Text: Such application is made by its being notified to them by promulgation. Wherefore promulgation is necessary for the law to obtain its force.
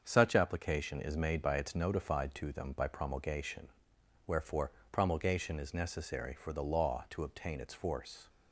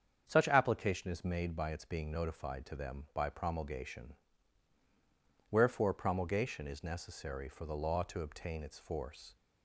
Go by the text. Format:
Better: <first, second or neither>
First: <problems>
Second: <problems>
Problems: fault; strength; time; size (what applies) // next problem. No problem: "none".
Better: second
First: starts louder than the rest; until 1.0 s; 7 dB // skips "being"; at 1.7 s // pauses between "Wherefore" and "promulgation"; slight; at 4.7 s; 0.20 s long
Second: starts louder than the rest; strong; until 1.2 s; 7.5 dB